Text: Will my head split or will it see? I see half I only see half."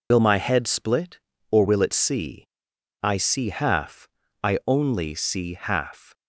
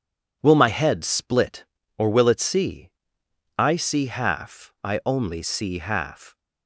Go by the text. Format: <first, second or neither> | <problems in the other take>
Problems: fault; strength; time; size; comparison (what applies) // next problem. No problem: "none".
second | loses the start of "Will"; at 0.1 s; 80 ms // pauses between "half" and "I"; slight; at 4.0 s; 0.34 s long